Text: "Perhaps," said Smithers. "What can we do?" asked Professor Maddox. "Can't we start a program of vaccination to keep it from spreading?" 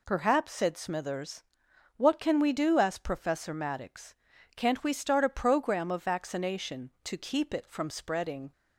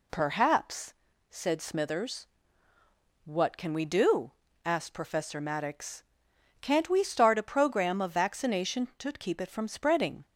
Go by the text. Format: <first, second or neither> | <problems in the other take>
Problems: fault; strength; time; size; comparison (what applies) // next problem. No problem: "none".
neither | none